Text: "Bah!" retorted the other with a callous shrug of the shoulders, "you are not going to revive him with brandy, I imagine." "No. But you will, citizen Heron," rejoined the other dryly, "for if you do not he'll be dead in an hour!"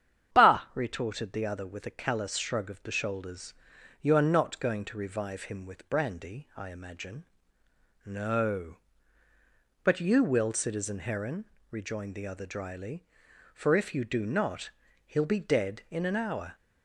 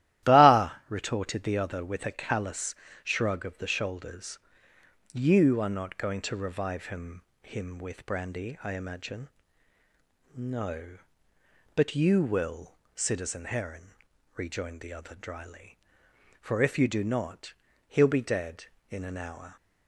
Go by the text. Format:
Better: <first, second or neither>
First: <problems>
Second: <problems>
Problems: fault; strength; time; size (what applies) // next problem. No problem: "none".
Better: first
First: starts louder than the rest; strong; until 1.4 s; 9 dB // pauses between "not" and "he'll"; slight; at 14.6 s; 0.36 s long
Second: starts louder than the rest; strong; until 1.3 s; 14 dB // pauses between "callous" and "shrug"; slight; at 2.7 s; 0.30 s long // says "him" twice; at 7.4 s // pauses between "not" and "he'll"; slight; at 17.5 s; 0.36 s long